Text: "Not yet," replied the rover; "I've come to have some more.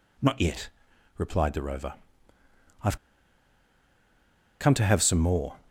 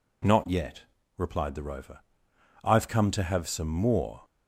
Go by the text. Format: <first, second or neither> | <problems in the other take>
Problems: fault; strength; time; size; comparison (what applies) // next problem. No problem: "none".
second | pauses between "I've" and "come"; strong; at 2.9 s; 1.6 s long